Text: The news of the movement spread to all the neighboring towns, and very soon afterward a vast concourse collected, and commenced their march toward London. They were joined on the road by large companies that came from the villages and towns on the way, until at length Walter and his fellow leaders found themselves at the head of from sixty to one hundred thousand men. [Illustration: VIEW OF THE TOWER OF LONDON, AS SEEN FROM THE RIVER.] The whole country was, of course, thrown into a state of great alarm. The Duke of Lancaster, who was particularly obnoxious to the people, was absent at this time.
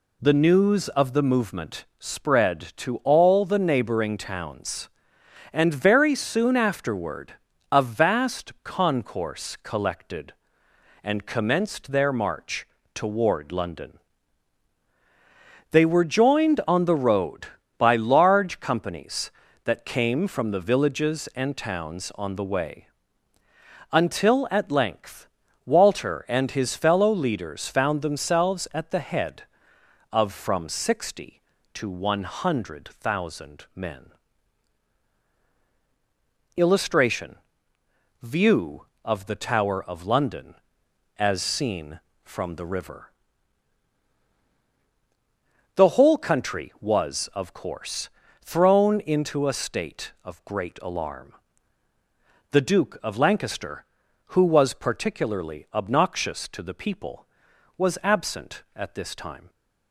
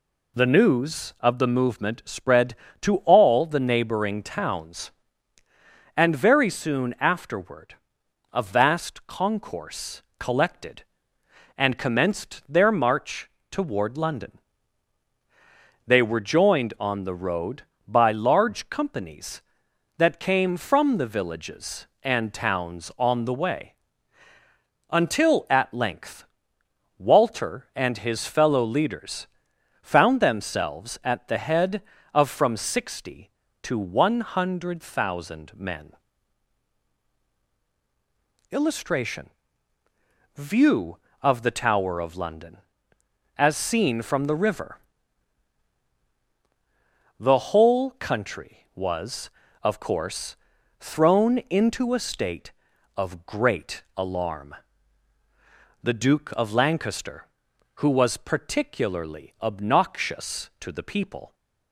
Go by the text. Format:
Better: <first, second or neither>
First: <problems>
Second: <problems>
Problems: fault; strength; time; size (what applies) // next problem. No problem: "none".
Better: first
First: pauses between "afterward" and "a"; slight; at 7.3 s; 0.36 s long // pauses between "march" and "toward"; slight; at 12.6 s; 0.26 s long // pauses between "length" and "Walter"; at 25.2 s; 0.38 s long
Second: pauses between "afterward" and "a"; noticeable; at 7.7 s; 0.56 s long // pauses between "concourse" and "collected"; slight; at 10.0 s; 0.16 s long // pauses between "march" and "toward"; slight; at 13.2 s; 0.22 s long // pauses between "length" and "Walter"; noticeable; at 26.2 s; 0.74 s long // pauses between "leaders" and "found"; noticeable; at 29.2 s; 0.52 s long // stops before "was absent at this time"; at 61.3 s